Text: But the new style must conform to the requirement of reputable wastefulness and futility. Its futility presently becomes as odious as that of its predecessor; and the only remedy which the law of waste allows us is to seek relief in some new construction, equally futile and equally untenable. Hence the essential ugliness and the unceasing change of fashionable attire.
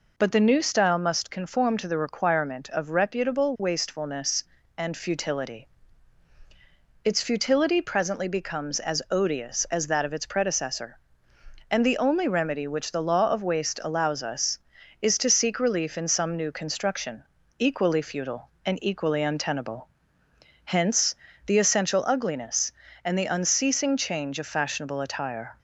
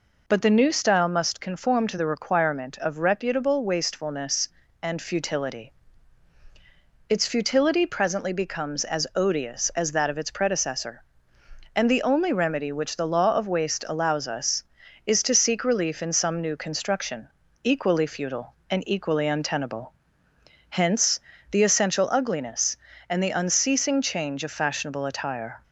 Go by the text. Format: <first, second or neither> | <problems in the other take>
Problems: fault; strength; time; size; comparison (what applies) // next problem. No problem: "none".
neither | pauses between "Hence" and "the"; slight; the same in both